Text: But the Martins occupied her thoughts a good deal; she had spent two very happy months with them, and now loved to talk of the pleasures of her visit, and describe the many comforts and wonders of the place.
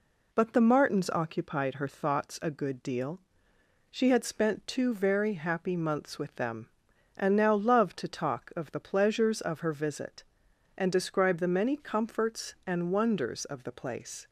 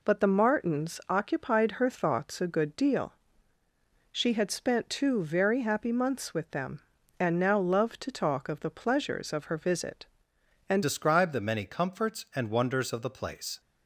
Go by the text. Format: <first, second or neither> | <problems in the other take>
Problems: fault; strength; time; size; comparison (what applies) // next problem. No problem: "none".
first | changes voice at "describe"; from 10.8 s on; 2.7 s long